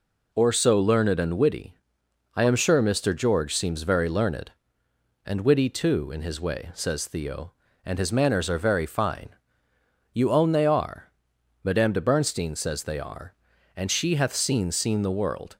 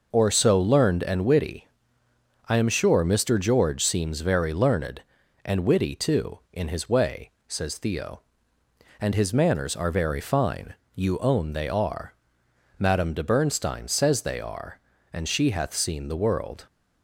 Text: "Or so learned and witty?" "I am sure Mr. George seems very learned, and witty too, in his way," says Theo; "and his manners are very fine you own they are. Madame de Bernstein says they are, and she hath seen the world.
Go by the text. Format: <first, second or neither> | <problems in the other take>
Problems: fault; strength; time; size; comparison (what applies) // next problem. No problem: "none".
second | pauses between "fine" and "you"; noticeable; at 9.3 s; 0.78 s long; slight in the second // says "seen" twice; at 14.7 s